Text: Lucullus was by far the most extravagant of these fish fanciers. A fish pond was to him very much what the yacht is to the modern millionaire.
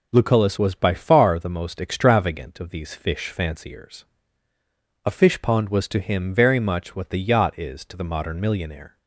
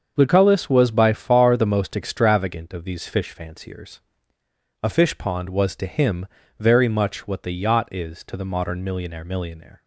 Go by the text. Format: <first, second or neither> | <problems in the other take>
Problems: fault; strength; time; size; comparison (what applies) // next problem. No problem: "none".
first | starts louder than the rest; until 1.1 s; 7 dB // pauses between "him" and "very"; slight; at 6.2 s; 0.32 s long // says "millionaire" twice; at 9.2 s